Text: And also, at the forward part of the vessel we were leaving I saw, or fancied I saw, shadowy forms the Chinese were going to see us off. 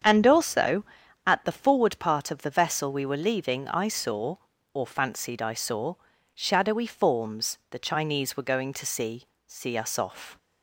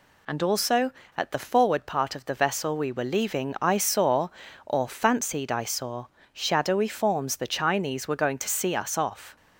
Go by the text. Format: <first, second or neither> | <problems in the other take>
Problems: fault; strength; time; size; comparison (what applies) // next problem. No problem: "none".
second | starts louder than the rest; strong; until 1.4 s; 7.5 dB // says "see" twice; at 9.4 s